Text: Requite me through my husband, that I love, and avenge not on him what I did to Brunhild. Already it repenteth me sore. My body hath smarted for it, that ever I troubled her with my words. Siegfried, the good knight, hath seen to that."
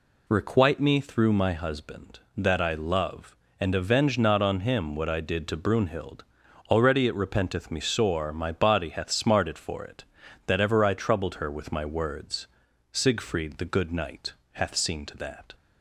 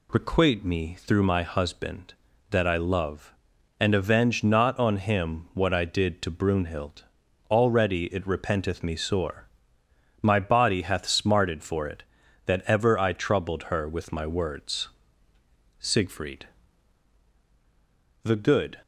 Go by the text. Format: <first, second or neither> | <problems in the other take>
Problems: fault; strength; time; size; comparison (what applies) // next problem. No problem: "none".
first | stops before "knight hath seen to that"; at 18.8 s